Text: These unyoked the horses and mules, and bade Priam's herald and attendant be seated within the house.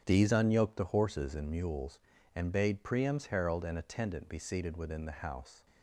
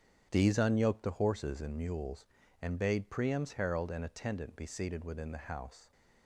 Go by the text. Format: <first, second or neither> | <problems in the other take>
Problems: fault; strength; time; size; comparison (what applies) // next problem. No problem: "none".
neither | starts louder than the rest; strong; the same in both